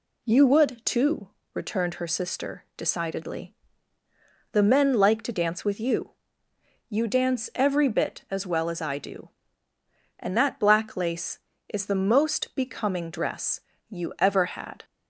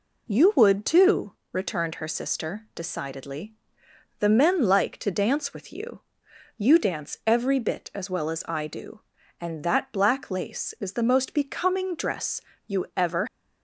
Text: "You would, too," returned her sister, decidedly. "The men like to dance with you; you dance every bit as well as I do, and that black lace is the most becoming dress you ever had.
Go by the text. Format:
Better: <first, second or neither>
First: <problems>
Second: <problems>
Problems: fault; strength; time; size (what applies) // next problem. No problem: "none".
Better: first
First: pauses between "dress" and "you"; slight; at 13.6 s; 0.26 s long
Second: pauses between "dress" and "you"; slight; at 12.4 s; 0.26 s long // stops before "had"; at 13.2 s